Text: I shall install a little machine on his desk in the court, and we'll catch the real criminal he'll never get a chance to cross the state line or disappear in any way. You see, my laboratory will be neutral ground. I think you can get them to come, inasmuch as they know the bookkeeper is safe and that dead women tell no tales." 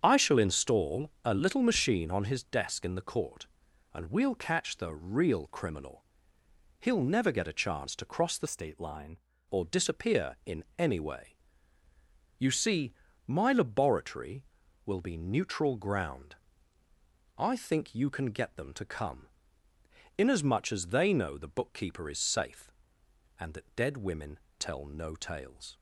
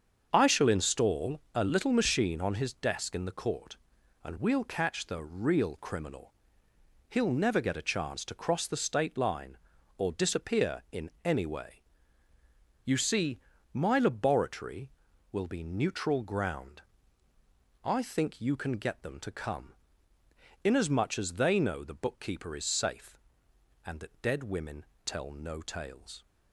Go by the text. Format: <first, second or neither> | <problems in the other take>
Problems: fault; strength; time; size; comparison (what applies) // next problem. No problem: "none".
second | starts louder than the rest; strong; until 1.0 s; 8 dB; also in the second // pauses between "criminal" and "he'll"; noticeable; at 6.0 s; 0.76 s long; noticeable in the second // changes voice from "state" to "line"; from 8.4 to 9.1 s; 0.7 s long // pauses between "women" and "tell"; slight; at 24.3 s; 0.22 s long; slight in the second